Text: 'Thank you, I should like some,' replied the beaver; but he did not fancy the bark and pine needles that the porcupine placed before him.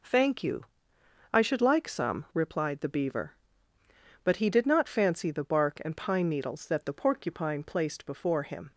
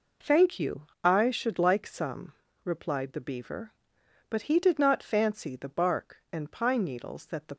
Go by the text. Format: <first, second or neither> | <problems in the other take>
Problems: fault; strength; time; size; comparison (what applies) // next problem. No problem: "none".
first | stops before "porcupine placed before him"; at 7.5 s